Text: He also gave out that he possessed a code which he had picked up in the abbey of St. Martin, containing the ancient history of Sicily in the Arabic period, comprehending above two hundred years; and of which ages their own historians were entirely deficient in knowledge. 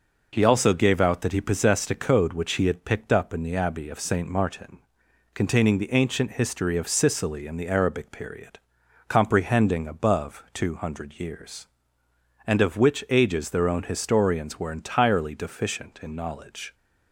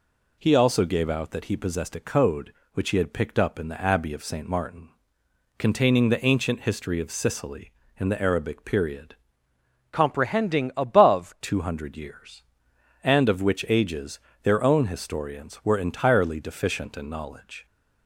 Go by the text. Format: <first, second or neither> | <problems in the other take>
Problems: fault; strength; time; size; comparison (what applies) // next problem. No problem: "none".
first | changes voice from "comprehending" to "above"; from 9.9 to 11.3 s; 1.4 s long // pauses between "ages" and "their"; slight; at 14.1 s; 0.24 s long